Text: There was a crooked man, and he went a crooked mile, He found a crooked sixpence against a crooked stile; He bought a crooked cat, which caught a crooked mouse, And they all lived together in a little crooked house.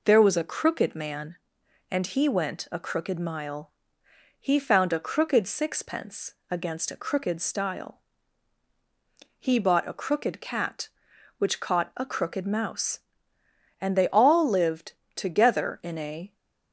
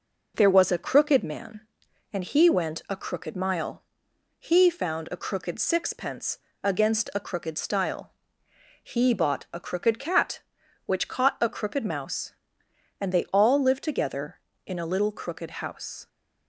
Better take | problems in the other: second | pauses between "sixpence" and "against"; slight; at 6.3 s; 0.16 s long; slight in the second // pauses between "lived" and "together"; slight; at 14.9 s; 0.22 s long // stops before "little crooked house"; at 16.3 s

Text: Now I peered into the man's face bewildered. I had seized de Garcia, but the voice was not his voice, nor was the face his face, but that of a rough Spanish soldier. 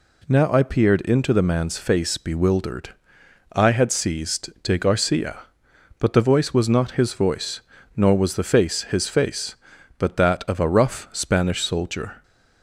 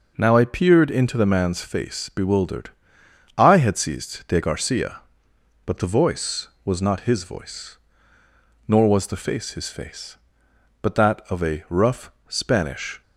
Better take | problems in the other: first | pauses between "rough" and "Spanish"; slight; at 12.1 s; 0.16 s long // stops before "soldier"; at 13.0 s

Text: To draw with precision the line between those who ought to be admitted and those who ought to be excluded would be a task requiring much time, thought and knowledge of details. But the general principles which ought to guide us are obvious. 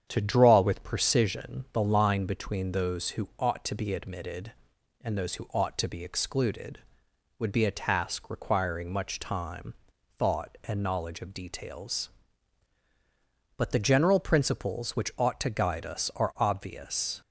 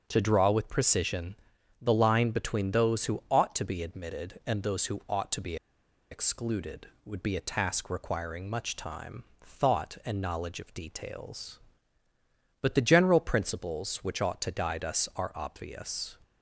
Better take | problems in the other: first | starts louder than the rest; strong; until 1.0 s; 7.5 dB; strong in the first // pauses between "precision" and "the"; at 1.3 s; 0.44 s long // pauses between "be" and "excluded"; noticeable; at 5.5 s; 0.55 s long

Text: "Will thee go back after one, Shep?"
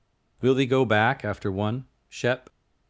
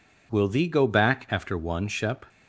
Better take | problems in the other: neither | none

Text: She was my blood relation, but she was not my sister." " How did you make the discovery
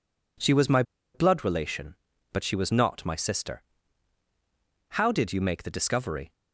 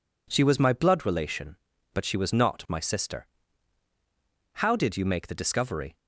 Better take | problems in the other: second | pauses between "my" and "blood"; slight; at 0.8 s; 0.31 s long

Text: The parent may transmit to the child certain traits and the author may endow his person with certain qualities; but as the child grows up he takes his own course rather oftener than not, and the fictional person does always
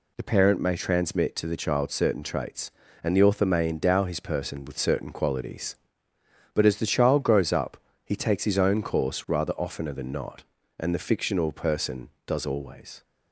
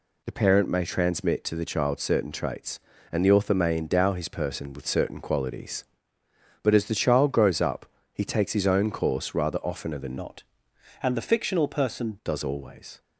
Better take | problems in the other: first | pauses between "up" and "he"; slight; at 7.8 s; 0.26 s long; slight in the first // changes voice from "not" to "person"; from 10.1 to 12.1 s; 2.0 s long

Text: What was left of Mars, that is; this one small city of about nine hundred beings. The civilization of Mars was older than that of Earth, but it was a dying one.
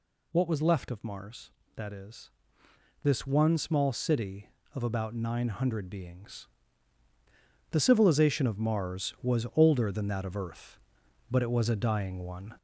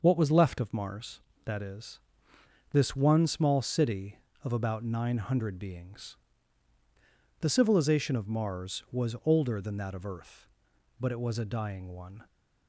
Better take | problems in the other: second | gets louder; throughout; 3.5 dB

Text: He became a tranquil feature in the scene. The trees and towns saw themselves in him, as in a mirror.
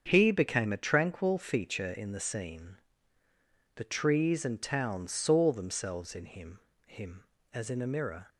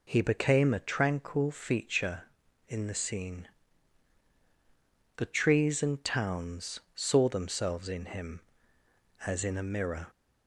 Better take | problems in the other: second | starts louder than the rest; until 1.0 s; 7 dB // says "him" twice; at 6.8 s

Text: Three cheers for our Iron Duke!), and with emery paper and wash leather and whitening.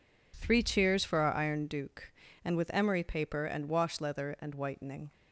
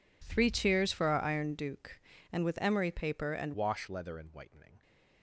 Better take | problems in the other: first | changes voice at "wash"; from 3.5 s on; 1.3 s long

